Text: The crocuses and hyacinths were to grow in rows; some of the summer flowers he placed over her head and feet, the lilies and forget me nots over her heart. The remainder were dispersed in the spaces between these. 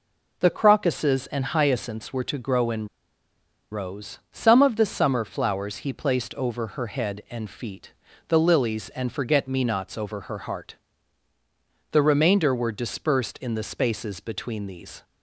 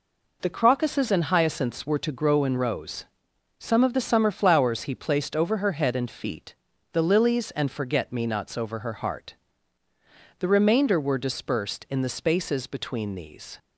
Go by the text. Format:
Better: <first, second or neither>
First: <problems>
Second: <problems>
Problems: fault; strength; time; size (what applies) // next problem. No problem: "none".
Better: second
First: pauses between "in" and "rows"; noticeable; at 2.8 s; 0.83 s long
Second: none